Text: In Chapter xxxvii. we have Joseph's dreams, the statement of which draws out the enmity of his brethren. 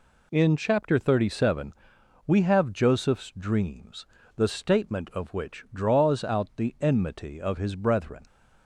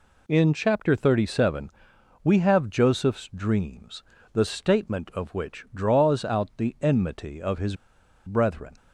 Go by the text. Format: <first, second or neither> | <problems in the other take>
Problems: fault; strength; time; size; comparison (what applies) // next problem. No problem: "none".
first | pauses between "his" and "brethren"; noticeable; at 7.7 s; 0.50 s long